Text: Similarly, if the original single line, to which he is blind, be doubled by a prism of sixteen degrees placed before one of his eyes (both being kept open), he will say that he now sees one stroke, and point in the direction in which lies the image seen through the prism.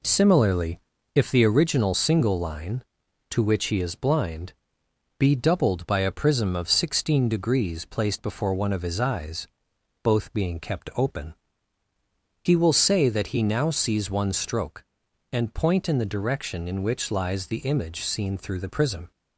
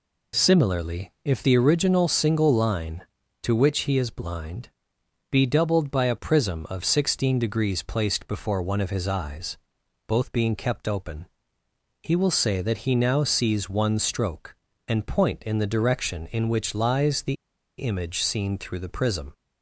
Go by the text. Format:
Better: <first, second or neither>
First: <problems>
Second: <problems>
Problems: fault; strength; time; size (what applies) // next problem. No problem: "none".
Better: first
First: none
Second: pauses between "the" and "image"; at 17.3 s; 0.43 s long